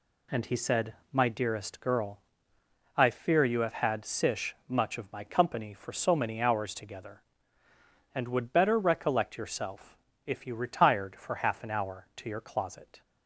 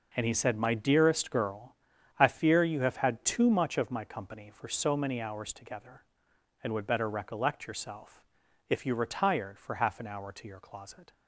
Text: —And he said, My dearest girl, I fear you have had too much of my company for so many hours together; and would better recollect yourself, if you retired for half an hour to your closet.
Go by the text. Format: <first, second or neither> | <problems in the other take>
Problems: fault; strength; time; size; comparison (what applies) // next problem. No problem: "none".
second | says "sish" for "too"; at 4.0 s